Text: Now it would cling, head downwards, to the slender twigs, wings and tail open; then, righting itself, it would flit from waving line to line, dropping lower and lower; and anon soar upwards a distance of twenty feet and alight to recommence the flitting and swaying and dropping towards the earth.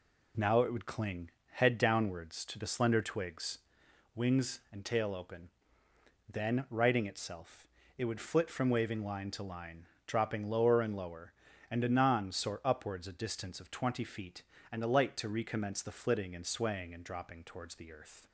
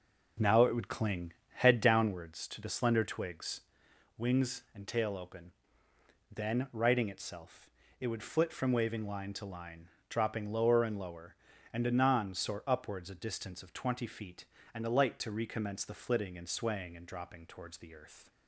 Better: first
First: none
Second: starts louder than the rest; noticeable; until 2.2 s; 5.5 dB

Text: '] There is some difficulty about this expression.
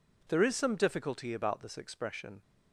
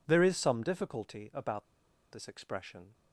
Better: first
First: none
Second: pauses between "about" and "this"; noticeable; at 1.6 s; 0.47 s long

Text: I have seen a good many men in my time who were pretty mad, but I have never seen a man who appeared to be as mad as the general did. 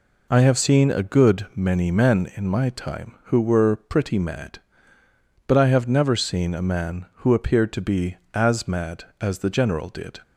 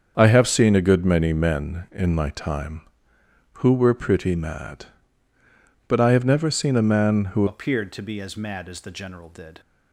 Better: first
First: none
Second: starts louder than the rest; strong; until 1.1 s; 7 dB // changes voice at "appeared"; from 7.4 s on; 2.2 s long

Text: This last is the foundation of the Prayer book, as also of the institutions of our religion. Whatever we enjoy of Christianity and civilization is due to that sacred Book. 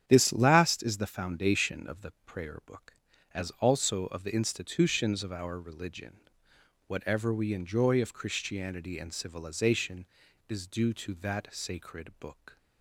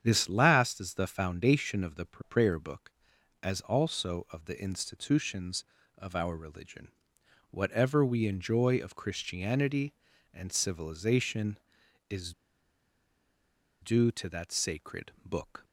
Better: first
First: starts louder than the rest; strong; until 1.0 s; 9.5 dB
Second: starts louder than the rest; strong; until 1.0 s; 8.5 dB // pauses between "is" and "due"; strong; at 12.3 s; 1.4 s long

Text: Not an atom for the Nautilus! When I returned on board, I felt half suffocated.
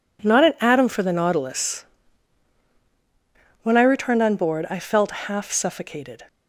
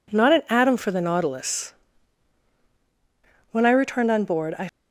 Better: first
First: none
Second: stops before "felt half suffocated"; at 4.6 s

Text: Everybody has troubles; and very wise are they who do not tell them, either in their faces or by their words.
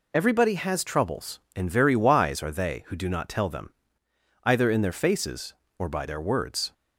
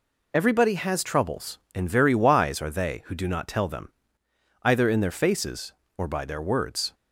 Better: neither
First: none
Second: none

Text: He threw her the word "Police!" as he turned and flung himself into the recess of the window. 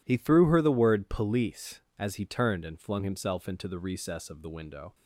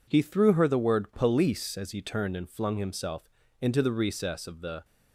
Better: first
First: none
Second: pauses between "himself" and "into"; slight; at 3.2 s; 0.32 s long // stops before "window"; at 4.8 s

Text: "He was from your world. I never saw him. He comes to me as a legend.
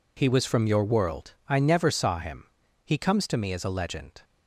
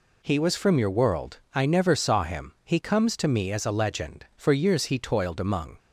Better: first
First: none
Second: goes on to say "For years he toiled among"; from 4.3 s on; 1.4 s long

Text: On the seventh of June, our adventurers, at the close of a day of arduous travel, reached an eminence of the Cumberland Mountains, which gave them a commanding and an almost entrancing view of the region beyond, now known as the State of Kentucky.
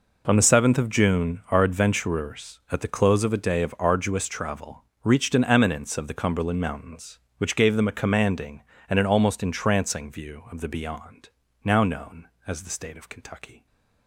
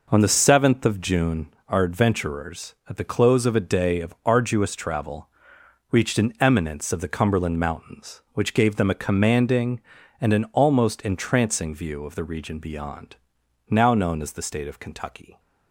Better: second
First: skips "region"; at 10.6 s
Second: none

